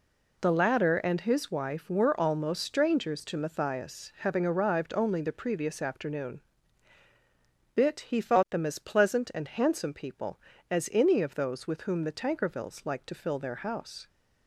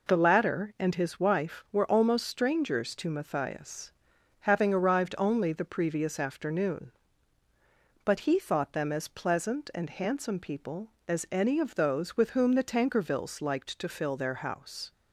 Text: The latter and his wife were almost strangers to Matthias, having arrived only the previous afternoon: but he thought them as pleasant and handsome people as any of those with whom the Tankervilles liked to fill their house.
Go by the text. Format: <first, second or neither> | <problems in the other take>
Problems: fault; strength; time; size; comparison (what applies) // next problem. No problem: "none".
second | says "bit" for "but"; at 7.7 s